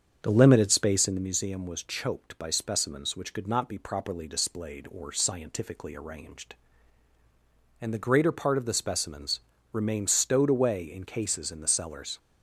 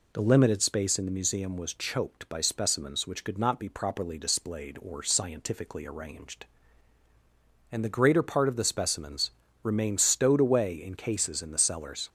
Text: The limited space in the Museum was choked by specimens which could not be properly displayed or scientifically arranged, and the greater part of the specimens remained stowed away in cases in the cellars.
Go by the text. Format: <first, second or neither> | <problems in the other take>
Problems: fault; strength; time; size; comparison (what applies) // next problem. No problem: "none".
second | starts louder than the rest; strong; until 1.3 s; 7.5 dB // pauses between "specimens" and "remained"; slight; at 9.3 s; 0.32 s long; slight in the second